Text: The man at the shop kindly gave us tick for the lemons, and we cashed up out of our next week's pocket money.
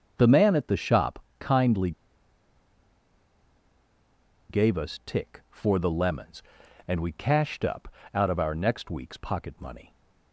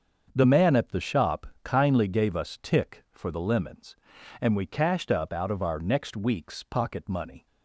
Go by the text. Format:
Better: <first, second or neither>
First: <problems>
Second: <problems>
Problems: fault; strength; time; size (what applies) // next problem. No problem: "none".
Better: second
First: starts louder than the rest; until 1.1 s; 6.5 dB // pauses between "shop" and "kindly"; slight; at 1.2 s; 0.16 s long // pauses between "kindly" and "gave"; strong; at 1.9 s; 2.5 s long // pauses between "up" and "out"; slight; at 7.8 s; 0.28 s long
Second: starts louder than the rest; until 1.3 s; 7 dB // pauses between "shop" and "kindly"; slight; at 1.4 s; 0.16 s long